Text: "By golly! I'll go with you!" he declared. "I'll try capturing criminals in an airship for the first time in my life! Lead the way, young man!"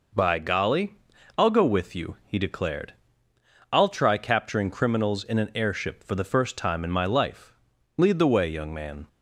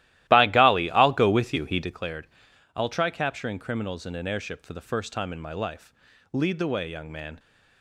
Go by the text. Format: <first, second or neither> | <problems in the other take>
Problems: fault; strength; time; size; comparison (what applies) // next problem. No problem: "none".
first | starts louder than the rest; strong; until 1.9 s; 15 dB